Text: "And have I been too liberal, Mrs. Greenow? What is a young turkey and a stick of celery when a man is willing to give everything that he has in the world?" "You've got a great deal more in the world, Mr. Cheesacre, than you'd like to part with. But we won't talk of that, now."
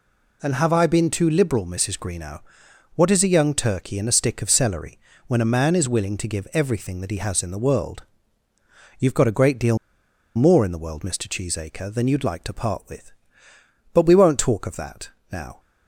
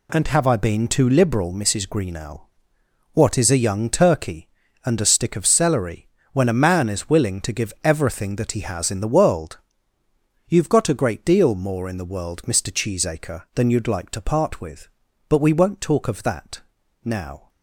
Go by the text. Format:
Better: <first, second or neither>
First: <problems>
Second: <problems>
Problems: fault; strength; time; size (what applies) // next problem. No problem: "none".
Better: second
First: pauses between "celery" and "when"; slight; at 4.9 s; 0.30 s long // pauses between "deal" and "more"; noticeable; at 9.7 s; 0.60 s long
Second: pauses between "celery" and "when"; slight; at 6.0 s; 0.24 s long